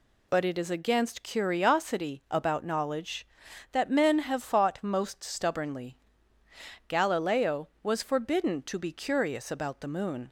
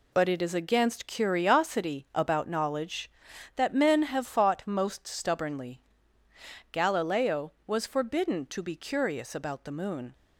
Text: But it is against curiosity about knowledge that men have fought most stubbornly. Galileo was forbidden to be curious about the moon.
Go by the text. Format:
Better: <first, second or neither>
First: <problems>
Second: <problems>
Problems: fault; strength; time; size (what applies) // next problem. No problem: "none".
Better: first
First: none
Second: gets quieter; strong; throughout; 7.5 dB